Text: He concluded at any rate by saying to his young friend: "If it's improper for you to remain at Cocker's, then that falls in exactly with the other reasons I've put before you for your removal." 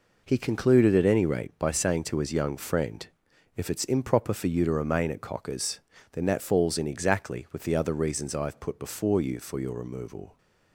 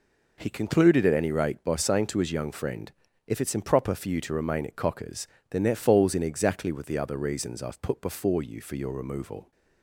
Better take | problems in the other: neither | none

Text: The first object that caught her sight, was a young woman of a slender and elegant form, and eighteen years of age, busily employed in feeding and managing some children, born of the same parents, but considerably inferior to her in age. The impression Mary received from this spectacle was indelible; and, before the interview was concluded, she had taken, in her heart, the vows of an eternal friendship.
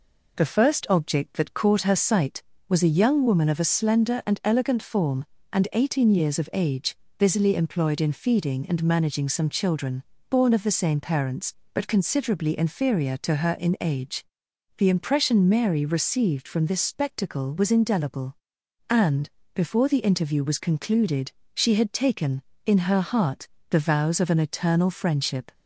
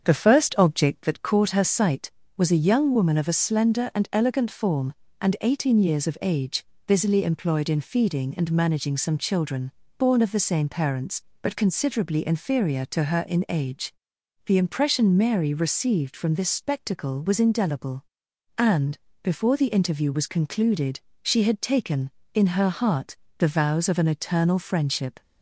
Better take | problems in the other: first | starts louder than the rest; strong; until 1.1 s; 7.5 dB

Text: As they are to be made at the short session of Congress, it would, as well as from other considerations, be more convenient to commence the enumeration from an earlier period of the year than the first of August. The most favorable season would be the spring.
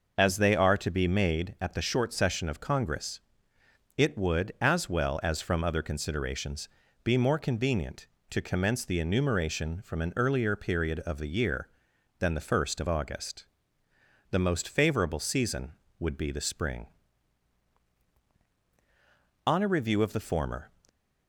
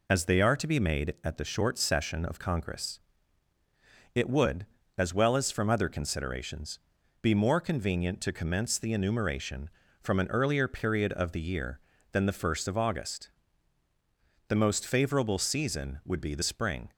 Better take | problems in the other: second | goes on to say "On a review of the former"; noticeable; from 19.4 s on; 1.2 s long

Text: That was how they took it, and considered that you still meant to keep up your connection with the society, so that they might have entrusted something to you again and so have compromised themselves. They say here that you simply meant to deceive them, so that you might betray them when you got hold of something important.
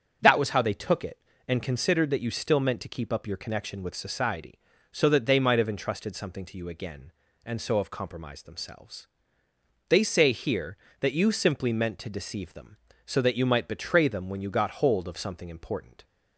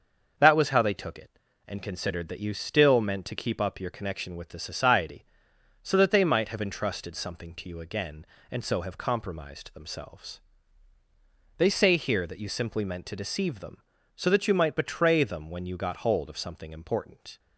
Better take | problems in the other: second | starts louder than the rest; until 1.2 s; 7 dB; also in the second // skips "the"; at 3.9 s

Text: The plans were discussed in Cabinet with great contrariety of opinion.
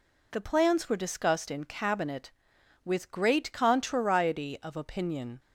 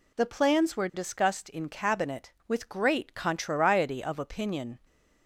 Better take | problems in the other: neither | none

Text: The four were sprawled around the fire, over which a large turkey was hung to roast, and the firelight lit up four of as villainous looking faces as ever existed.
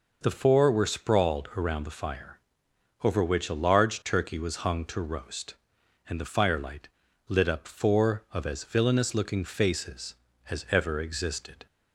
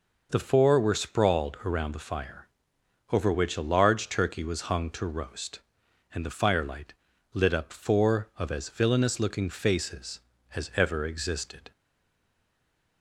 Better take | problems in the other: first | pauses between "firelight" and "lit"; at 6.9 s; 0.40 s long; also in the first // stays silent after the last word; noticeable; from 11.7 s on; 1.3 s long

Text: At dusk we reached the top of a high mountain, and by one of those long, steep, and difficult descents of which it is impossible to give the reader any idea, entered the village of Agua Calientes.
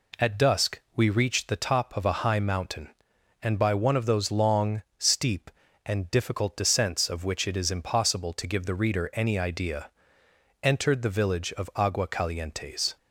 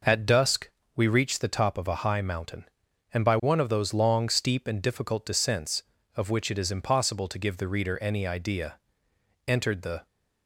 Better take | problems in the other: first | pauses between "dusk" and "we"; slight; at 0.6 s; 0.28 s long // stops before "village of Agua Calientes"; at 10.0 s

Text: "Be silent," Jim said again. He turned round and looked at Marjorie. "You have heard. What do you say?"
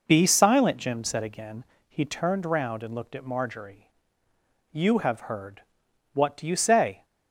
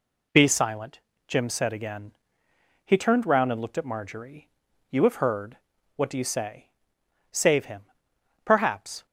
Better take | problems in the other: first | goes on to say "Save him Perhaps"; strong; from 7.3 s on; 1.7 s long

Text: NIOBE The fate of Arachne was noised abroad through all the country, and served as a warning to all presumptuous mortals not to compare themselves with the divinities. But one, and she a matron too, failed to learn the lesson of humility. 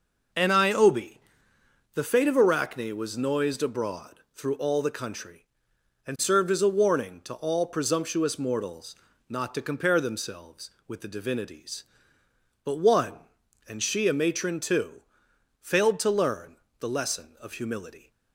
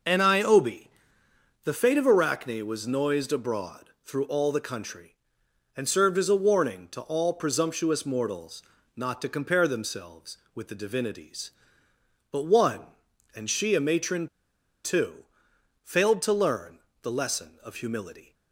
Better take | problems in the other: first | pauses between "NIOBE" and "The"; noticeable; at 0.8 s; 0.76 s long; noticeable in the first // pauses between "mortals" and "not"; slight; at 8.6 s; 0.32 s long; slight in the first // pauses between "matron" and "too"; noticeable; at 14.2 s; 0.58 s long // pauses between "learn" and "the"; slight; at 16.7 s; 0.24 s long; slight in the first

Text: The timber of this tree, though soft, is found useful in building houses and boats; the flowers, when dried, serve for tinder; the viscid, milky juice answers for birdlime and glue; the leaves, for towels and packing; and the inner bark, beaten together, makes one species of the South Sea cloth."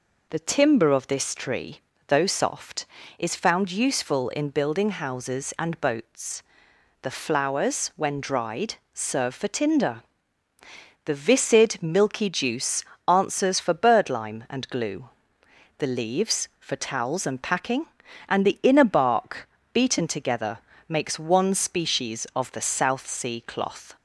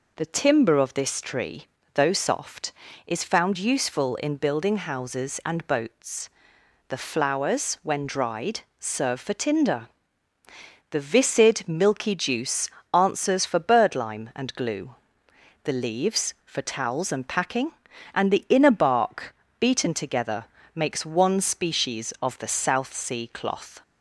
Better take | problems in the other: neither | pauses between "juice" and "answers"; slight; the same in both

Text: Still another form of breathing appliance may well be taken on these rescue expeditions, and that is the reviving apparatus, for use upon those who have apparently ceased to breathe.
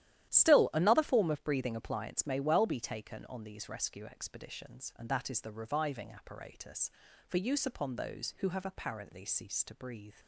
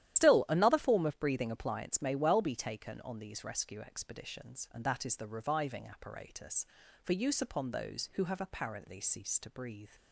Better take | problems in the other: first | loses the start of "Still"; at 0.1 s; 100 ms // starts louder than the rest; strong; until 1.2 s; 12 dB; strong in the first

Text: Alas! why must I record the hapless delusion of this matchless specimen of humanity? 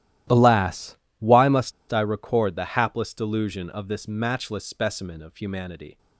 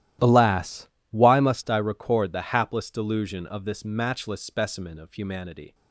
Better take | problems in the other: second | starts louder than the rest; strong; until 1.5 s; 13.5 dB; strong in the second // pauses between "must" and "I"; slight; at 1.7 s; 0.20 s long

